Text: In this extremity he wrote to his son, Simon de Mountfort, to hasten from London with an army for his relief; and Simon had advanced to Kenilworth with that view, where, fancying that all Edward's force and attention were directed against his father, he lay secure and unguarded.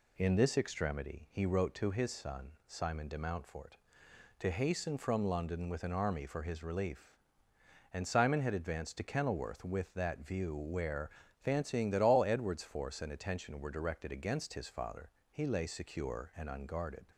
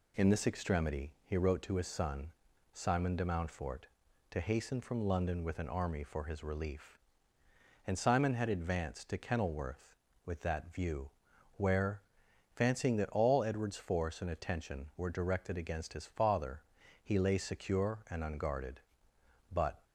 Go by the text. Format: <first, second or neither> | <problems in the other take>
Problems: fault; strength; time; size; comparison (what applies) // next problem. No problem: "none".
first | goes on to say "But"; slight; from 19.5 s on; 0.32 s long